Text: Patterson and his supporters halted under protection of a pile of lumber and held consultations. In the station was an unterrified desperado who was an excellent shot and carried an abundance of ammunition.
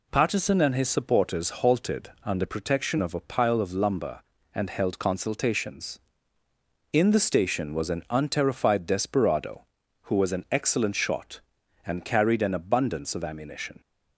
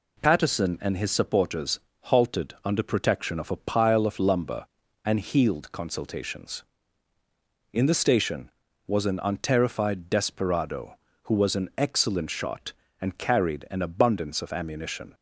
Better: first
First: none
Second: pauses between "supporters" and "halted"; slight; at 1.7 s; 0.24 s long // says "healed" for "held"; at 5.2 s

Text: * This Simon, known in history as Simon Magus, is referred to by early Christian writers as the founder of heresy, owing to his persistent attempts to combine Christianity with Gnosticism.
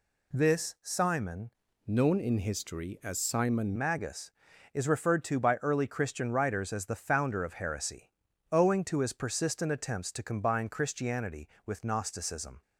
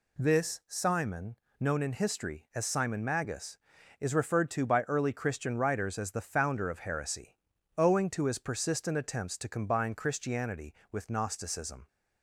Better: second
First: changes voice from "known" to "Simon"; from 1.8 to 3.7 s; 1.9 s long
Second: none

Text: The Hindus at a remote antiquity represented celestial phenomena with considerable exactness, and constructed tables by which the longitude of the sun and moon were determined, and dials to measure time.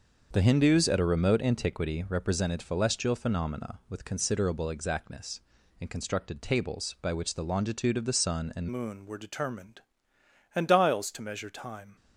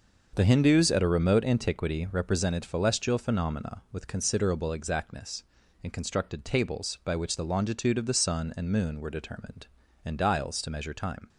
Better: second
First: starts louder than the rest; until 1.3 s; 6.5 dB // changes voice at "moon"; from 8.6 s on; 3.3 s long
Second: starts louder than the rest; until 1.3 s; 6 dB

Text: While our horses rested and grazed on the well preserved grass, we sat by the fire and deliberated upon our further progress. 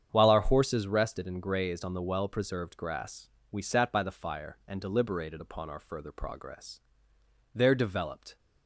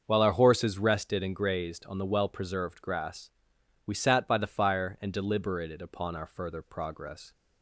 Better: second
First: starts louder than the rest; strong; until 1.1 s; 8.5 dB // goes on to say "There developed"; noticeable; from 7.5 s on; 0.84 s long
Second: starts louder than the rest; until 1.0 s; 6.5 dB

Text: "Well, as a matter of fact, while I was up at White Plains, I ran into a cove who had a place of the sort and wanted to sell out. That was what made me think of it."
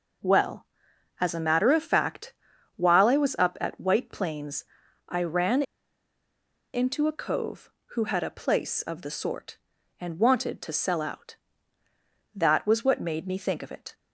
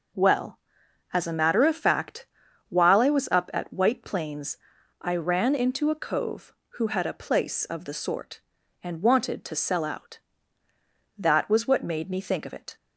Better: second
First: pauses between "ran" and "into"; at 5.6 s; 1.1 s long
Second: none

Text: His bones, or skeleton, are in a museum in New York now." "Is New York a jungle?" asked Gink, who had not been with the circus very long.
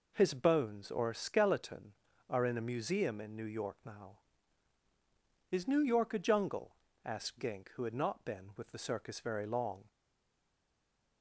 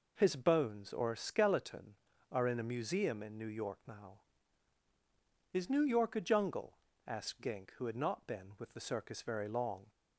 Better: second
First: stays silent after the last word; noticeable; from 9.8 s on; 1.4 s long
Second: none

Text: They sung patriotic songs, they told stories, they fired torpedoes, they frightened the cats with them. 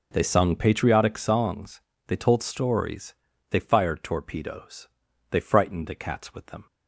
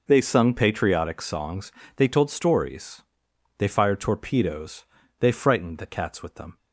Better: neither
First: none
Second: none

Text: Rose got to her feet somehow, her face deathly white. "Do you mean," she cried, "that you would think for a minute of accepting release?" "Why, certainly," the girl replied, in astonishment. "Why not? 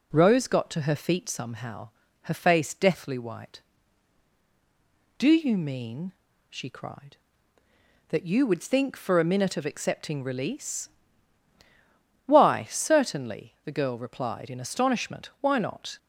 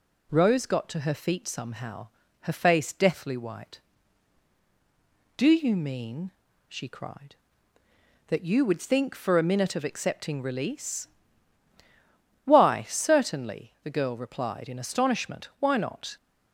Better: second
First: starts louder than the rest; slight; until 1.5 s; 2.5 dB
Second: none

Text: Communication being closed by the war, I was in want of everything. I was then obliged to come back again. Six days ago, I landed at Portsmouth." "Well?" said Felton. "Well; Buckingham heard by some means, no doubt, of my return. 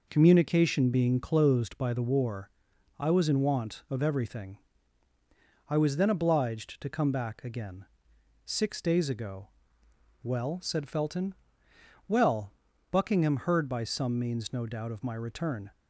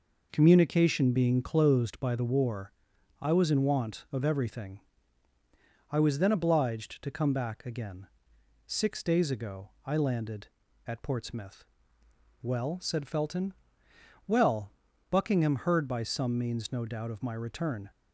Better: second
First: skips "I landed at Portsmouth"; at 9.8 s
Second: none

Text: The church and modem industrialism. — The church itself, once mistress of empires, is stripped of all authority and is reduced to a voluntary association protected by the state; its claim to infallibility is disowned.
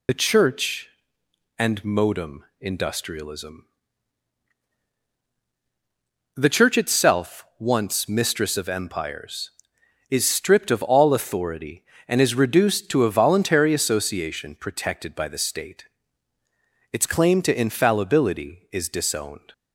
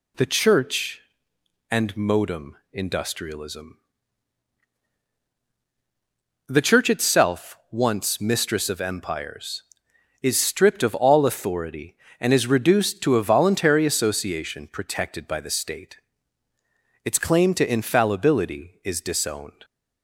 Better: second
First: loses the start of "The"; at 0.0 s; 50 ms // pauses between "modem" and "industrialism"; slight; at 2.4 s; 0.18 s long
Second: pauses between "modem" and "industrialism"; slight; at 2.5 s; 0.18 s long

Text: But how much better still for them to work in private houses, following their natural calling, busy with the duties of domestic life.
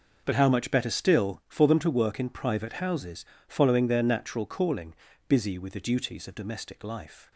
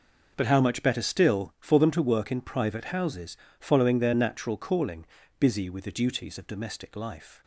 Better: neither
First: none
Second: none

